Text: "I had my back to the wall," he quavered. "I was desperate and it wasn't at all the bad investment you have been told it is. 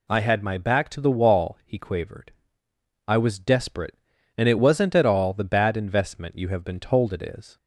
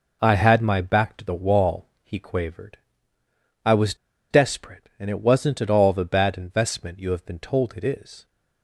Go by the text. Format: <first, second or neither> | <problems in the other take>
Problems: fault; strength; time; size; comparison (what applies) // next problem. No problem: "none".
first | pauses between "was" and "desperate"; at 3.9 s; 0.36 s long